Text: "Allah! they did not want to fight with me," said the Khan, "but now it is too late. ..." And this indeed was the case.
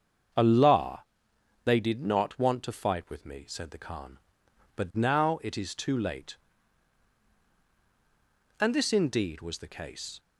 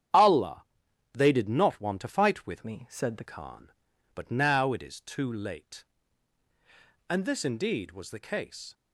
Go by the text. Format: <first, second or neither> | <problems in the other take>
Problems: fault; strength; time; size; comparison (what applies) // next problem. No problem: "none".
first | starts louder than the rest; strong; until 1.6 s; 10 dB; strong in the first // changes voice from "me" to "the"; from 2.6 to 3.2 s; 0.6 s long